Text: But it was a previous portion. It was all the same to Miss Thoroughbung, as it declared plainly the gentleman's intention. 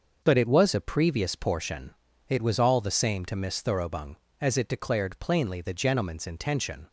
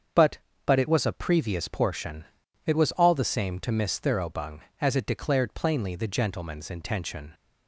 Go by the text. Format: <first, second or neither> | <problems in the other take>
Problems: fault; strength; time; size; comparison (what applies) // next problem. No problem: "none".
first | starts louder than the rest; strong; until 1.4 s; 7 dB; also in the first // says "But" twice; at 0.6 s